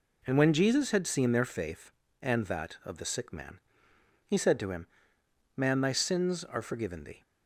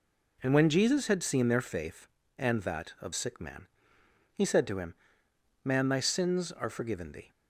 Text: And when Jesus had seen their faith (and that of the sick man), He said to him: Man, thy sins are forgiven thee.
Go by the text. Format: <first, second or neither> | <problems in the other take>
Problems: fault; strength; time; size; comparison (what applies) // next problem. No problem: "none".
first | skips "the"; at 3.1 s